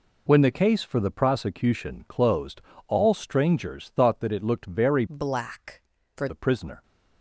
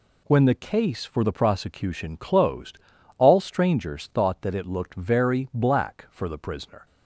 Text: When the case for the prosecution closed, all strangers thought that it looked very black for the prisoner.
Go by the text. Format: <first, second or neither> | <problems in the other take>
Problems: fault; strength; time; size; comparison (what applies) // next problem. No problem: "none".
second | changes voice from "black" to "for"; from 5.0 to 6.2 s; 1.2 s long